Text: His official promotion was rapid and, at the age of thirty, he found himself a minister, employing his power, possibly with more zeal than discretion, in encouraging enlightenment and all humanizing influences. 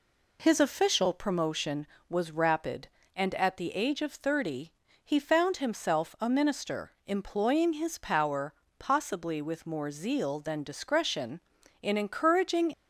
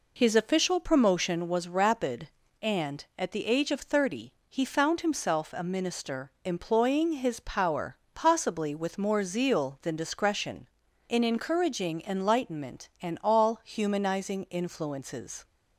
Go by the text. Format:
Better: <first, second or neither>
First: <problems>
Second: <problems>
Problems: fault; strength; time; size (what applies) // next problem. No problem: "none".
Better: second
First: stops before "enlightenment and all humanizing influences"; at 12.7 s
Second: none